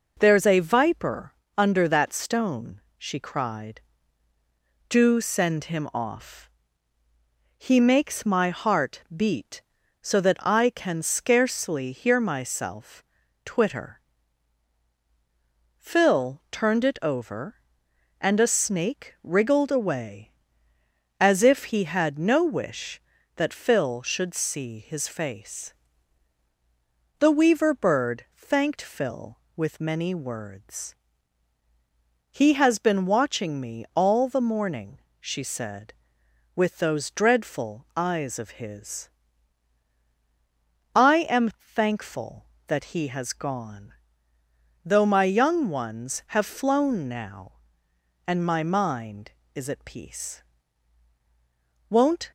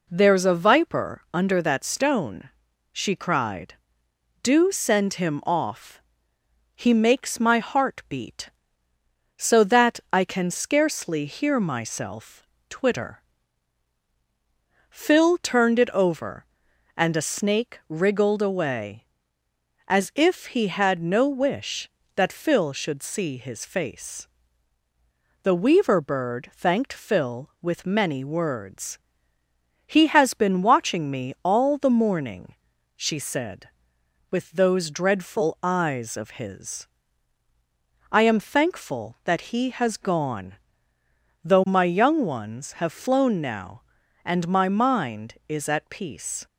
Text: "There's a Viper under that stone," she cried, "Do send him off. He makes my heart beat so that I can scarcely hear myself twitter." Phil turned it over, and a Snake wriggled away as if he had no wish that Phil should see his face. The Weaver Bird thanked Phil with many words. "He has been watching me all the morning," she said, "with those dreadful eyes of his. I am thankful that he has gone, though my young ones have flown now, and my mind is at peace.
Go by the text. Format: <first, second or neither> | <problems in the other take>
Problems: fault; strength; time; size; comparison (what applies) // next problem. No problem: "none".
second | pauses between "Viper" and "under"; slight; at 1.3 s; 0.22 s long // pauses between "myself" and "twitter"; at 13.0 s; 0.42 s long; slight in the second // goes on to say "Won't"; slight; from 51.8 s on; 0.42 s long